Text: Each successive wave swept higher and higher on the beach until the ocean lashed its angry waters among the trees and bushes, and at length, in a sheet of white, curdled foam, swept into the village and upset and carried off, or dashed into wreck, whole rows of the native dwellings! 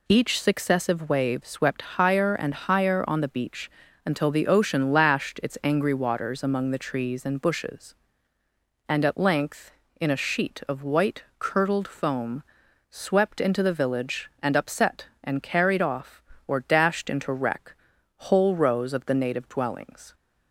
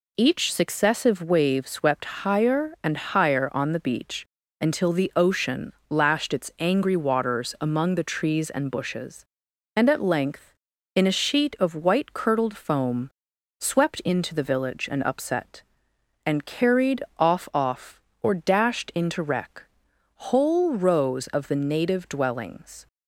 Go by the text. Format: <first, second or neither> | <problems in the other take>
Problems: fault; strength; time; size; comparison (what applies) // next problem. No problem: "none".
first | pauses between "beach" and "until"; slight; at 4.2 s; 0.36 s long; slight in the first // pauses between "ocean" and "lashed"; slight; at 5.7 s; 0.16 s long // says "off" twice; at 17.5 s